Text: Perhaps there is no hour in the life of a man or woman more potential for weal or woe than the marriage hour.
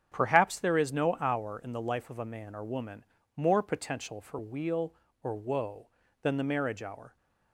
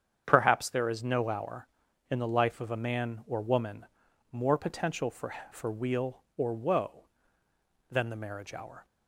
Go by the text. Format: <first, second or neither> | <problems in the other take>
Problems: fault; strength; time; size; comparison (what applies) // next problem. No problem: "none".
first | starts louder than the rest; strong; until 1.2 s; 8 dB; strong in the first // pauses between "woman" and "more"; noticeable; at 3.8 s; 0.46 s long; slight in the first // says "for" twice; at 5.5 s